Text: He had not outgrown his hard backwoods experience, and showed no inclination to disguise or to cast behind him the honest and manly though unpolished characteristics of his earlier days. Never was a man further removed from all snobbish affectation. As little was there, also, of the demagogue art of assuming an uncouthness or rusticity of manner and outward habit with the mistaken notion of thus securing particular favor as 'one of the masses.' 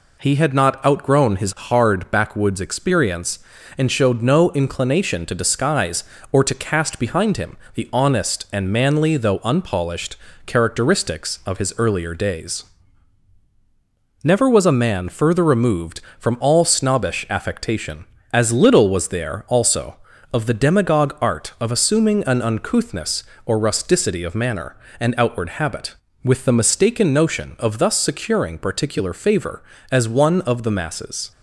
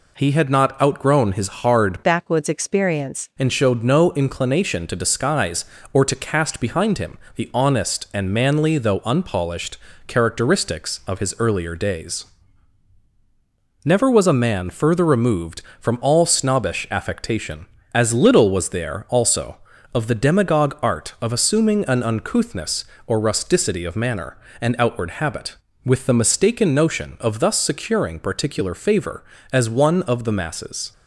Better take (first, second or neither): first